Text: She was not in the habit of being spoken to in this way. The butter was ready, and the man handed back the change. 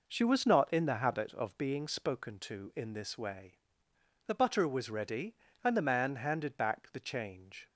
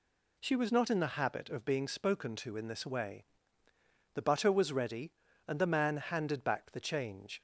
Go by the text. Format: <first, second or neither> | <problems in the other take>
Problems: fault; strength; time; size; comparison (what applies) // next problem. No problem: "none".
neither | none